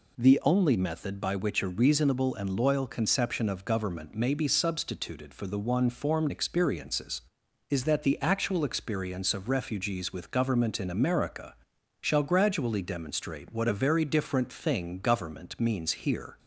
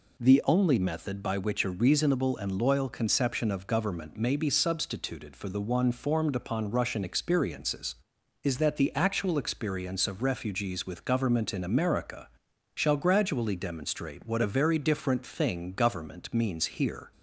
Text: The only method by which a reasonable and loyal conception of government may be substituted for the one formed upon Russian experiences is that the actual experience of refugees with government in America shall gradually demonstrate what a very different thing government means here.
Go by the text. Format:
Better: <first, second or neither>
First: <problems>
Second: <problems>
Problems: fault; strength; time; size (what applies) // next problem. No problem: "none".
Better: second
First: skips "upon Russian"; at 6.3 s // pauses between "America" and "shall"; noticeable; at 11.5 s; 0.46 s long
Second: pauses between "America" and "shall"; noticeable; at 12.2 s; 0.46 s long